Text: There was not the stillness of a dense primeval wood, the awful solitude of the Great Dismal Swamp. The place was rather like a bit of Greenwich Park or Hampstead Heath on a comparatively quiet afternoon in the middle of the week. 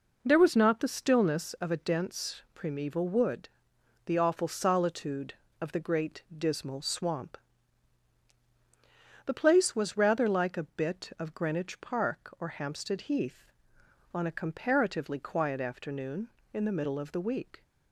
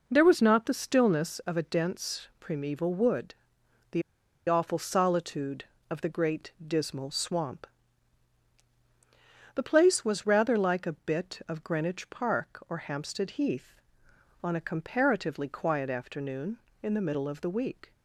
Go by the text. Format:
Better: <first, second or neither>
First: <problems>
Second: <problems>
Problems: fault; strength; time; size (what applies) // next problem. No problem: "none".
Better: first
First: none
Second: pauses between "the" and "awful"; noticeable; at 4.0 s; 0.46 s long